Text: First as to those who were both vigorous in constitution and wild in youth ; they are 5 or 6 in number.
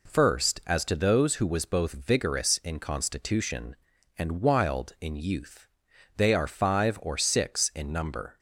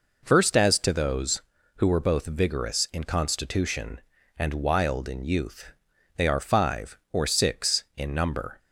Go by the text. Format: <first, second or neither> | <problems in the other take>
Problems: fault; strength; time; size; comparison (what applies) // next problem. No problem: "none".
second | says "was" for "were"; at 1.4 s